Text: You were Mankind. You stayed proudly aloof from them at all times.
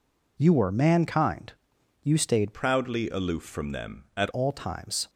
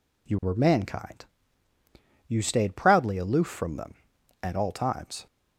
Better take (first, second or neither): second